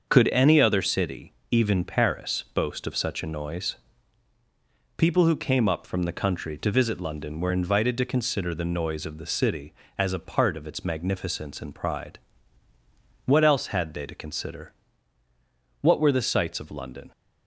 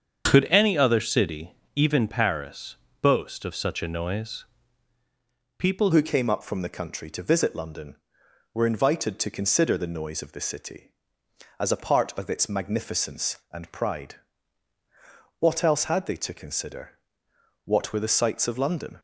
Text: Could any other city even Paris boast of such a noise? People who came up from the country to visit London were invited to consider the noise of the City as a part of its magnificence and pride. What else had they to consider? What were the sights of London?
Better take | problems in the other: first | starts louder than the rest; strong; until 1.2 s; 7 dB; also in the first // pauses between "city" and "even"; slight; at 1.5 s; 0.22 s long; slight in the first // pauses between "Paris" and "boast"; slight; at 2.7 s; 0.26 s long // changes voice at "who"; from 5.9 s on; 13.0 s long

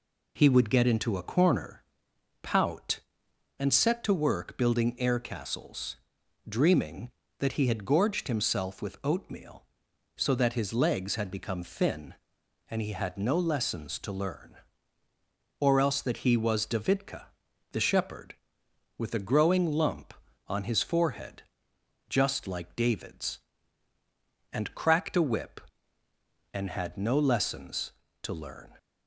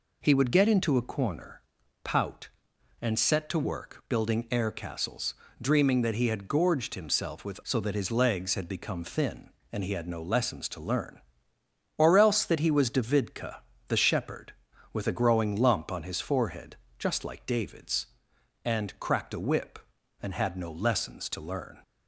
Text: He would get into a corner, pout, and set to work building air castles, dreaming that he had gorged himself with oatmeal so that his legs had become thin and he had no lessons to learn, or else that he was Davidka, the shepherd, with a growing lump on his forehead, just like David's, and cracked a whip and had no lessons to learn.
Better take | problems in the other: first | skips "oatmeal"; at 7.6 s

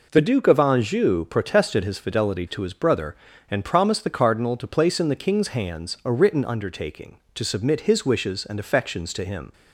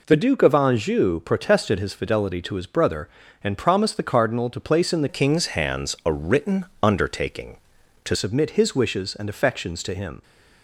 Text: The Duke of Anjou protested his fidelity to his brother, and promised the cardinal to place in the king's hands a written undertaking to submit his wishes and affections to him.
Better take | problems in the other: first | changes voice from "king's" to "to"; from 5.0 to 8.1 s; 3.1 s long // pauses between "written" and "undertaking"; slight; at 6.6 s; 0.16 s long

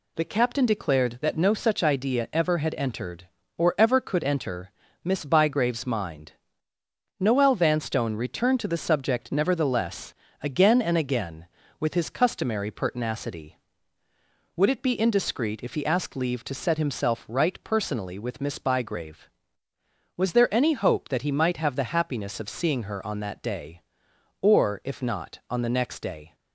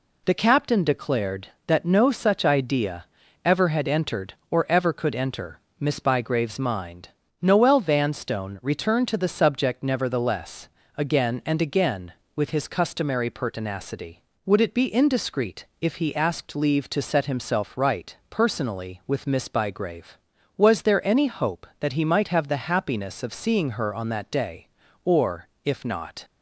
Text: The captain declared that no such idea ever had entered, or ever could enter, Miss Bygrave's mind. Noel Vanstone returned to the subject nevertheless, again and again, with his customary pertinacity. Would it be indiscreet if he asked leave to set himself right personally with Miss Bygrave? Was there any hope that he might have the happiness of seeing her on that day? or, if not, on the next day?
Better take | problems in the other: first | pauses between "idea" and "ever"; at 3.0 s; 0.40 s long // pauses between "indiscreet" and "if"; slight; at 15.6 s; 0.16 s long // pauses between "right" and "personally"; slight; at 18.1 s; 0.16 s long // stops before "on the next day"; at 26.2 s

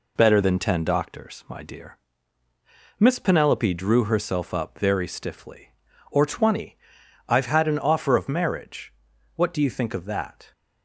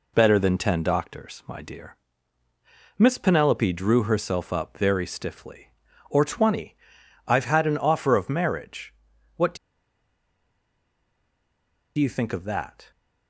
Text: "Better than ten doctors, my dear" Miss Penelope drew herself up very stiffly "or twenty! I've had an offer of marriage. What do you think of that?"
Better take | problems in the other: first | pauses between "dear" and "Miss"; at 1.9 s; 1.0 s long; also in the first // pauses between "do" and "you"; strong; at 9.5 s; 2.4 s long

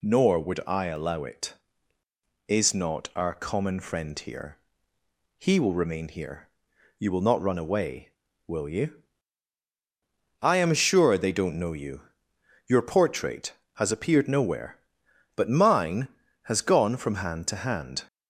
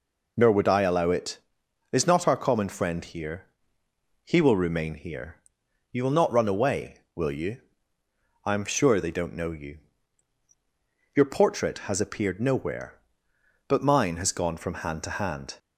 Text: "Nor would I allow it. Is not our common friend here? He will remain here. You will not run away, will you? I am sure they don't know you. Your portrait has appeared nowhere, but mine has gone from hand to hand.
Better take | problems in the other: neither | none

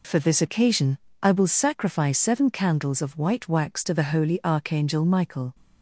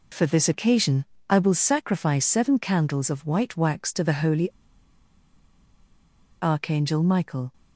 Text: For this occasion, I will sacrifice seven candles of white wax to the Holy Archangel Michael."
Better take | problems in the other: first | pauses between "Holy" and "Archangel"; strong; at 4.5 s; 1.9 s long

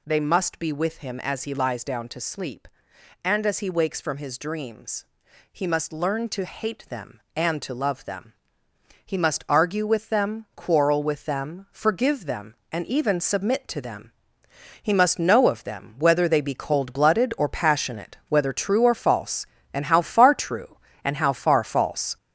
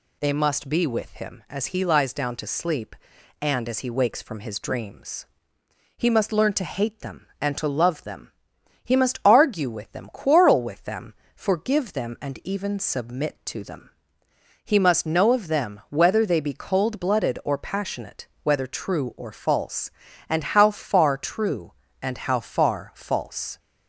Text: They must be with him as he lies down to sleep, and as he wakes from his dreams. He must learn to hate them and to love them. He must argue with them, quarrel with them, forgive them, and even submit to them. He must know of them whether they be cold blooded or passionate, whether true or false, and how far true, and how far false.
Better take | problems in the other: second | gets louder; noticeable; throughout; 6 dB

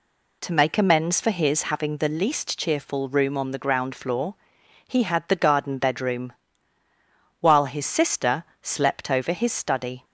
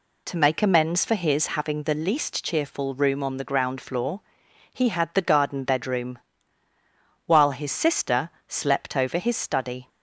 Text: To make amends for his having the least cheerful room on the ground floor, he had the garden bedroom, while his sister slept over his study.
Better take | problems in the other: neither | pauses between "sister" and "slept"; slight; the same in both

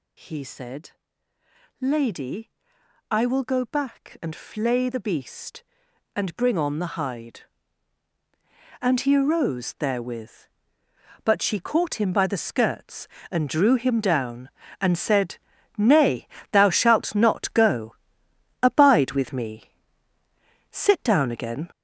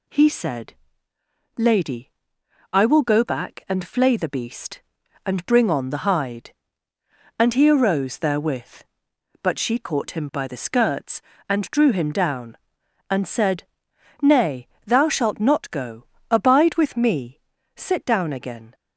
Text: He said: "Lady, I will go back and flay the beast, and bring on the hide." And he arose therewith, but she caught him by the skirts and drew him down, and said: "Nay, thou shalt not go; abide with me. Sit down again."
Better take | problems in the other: second | gets louder; noticeable; throughout; 6 dB

